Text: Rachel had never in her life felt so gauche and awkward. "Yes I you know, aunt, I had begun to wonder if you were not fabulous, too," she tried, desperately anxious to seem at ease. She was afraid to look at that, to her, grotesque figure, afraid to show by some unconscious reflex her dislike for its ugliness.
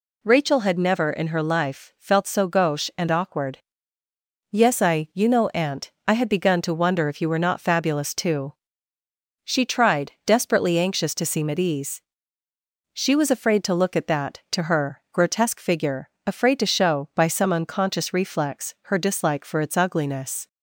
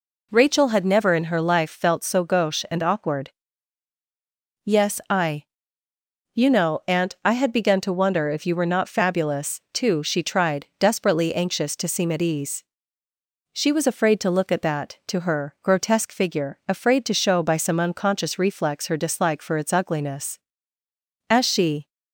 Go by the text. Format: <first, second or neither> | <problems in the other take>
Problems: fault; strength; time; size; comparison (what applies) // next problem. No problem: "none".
first | pauses between "I" and "you"; noticeable; at 5.4 s; 0.90 s long // goes on to say "As she"; from 21.3 s on; 0.58 s long